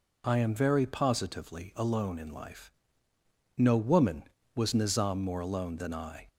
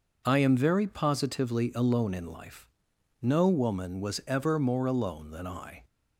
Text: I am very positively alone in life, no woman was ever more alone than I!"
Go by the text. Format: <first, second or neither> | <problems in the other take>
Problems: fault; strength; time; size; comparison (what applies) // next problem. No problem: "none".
second | says "nizam" for "ever"; at 4.7 s